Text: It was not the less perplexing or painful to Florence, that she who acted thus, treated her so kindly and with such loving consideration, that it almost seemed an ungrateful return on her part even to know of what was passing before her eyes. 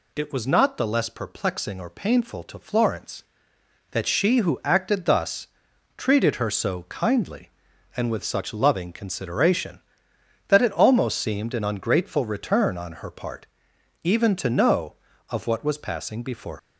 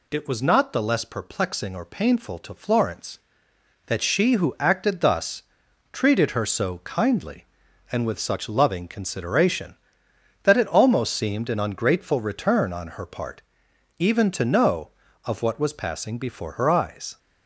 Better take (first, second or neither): second